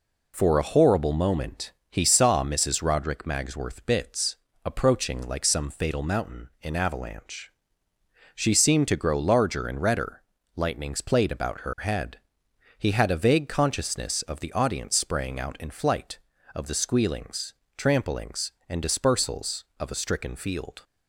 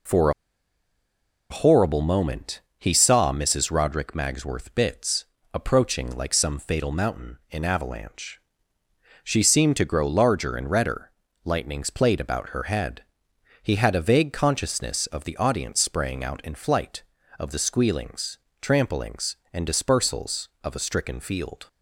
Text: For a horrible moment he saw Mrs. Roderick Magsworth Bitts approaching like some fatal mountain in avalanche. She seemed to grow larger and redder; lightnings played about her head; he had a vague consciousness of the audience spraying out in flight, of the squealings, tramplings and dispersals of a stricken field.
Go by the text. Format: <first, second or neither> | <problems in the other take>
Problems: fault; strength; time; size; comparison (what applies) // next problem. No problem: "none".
first | pauses between "For" and "a"; at 0.3 s; 1.1 s long // pauses between "moment" and "he"; slight; at 2.5 s; 0.18 s long; slight in the first // pauses between "Bitts" and "approaching"; slight; at 5.2 s; 0.30 s long; slight in the first